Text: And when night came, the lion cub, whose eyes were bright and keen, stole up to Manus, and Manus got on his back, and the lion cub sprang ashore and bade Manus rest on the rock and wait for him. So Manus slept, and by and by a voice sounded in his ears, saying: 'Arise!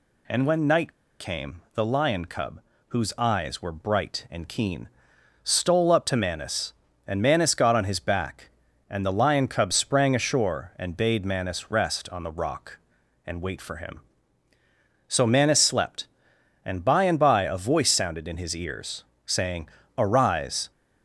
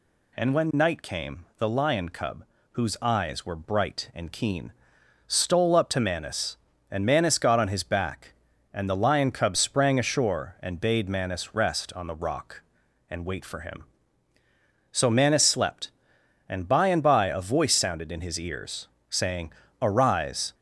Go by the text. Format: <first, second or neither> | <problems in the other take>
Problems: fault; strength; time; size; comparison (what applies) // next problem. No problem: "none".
second | pauses between "night" and "came"; slight; at 0.9 s; 0.27 s long